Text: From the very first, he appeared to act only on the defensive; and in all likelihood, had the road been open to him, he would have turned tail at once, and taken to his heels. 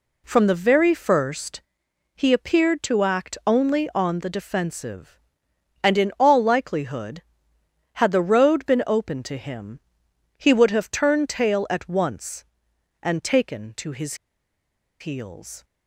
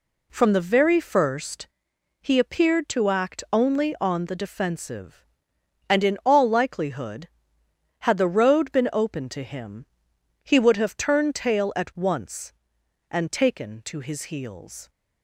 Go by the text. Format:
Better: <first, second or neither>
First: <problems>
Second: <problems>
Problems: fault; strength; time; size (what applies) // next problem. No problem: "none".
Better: second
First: pauses between "his" and "heels"; noticeable; at 14.1 s; 0.85 s long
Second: none